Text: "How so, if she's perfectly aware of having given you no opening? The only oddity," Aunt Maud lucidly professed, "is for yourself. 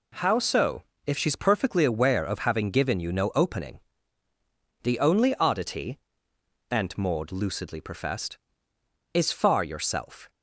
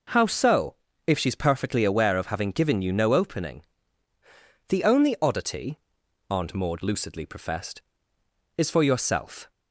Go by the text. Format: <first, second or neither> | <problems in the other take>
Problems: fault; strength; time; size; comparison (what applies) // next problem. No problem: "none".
second | says "far" for "for"; at 9.3 s